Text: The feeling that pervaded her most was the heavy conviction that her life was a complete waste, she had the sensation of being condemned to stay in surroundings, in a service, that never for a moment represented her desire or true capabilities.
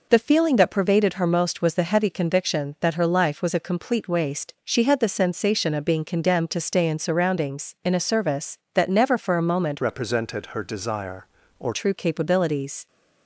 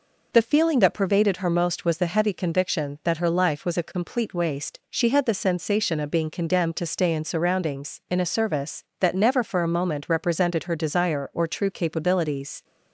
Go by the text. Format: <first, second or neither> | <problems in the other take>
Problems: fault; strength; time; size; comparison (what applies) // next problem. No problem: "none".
second | changes voice from "represented" to "or"; from 9.8 to 11.7 s; 1.9 s long